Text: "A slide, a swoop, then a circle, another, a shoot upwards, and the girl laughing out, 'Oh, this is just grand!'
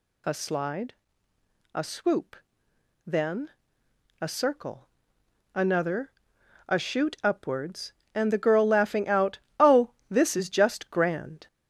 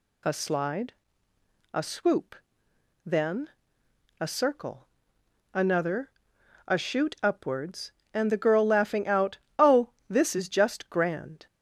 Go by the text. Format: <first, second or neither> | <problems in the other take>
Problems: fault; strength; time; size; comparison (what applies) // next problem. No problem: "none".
second | gets louder; noticeable; throughout; 5 dB // pauses between "then" and "a"; noticeable; at 3.5 s; 0.68 s long; noticeable in the second